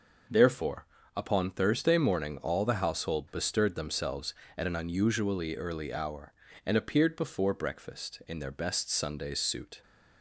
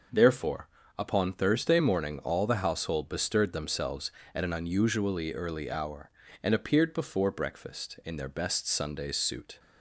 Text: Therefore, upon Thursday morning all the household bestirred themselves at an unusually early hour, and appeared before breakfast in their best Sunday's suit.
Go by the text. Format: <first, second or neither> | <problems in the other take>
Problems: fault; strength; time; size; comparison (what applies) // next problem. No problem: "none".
neither | none